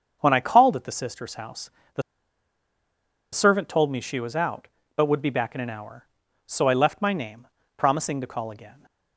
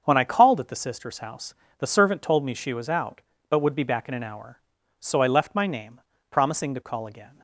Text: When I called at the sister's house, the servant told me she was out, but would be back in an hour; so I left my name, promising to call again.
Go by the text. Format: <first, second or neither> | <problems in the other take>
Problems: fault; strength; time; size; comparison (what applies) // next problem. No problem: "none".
second | starts louder than the rest; until 1.2 s; 7 dB; also in the second // pauses between "the" and "servant"; strong; at 2.0 s; 1.3 s long